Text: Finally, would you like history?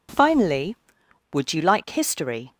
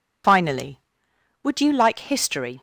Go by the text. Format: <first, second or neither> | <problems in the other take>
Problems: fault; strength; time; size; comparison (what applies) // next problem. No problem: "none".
first | loses the start of "Finally"; at 0.2 s; 60 ms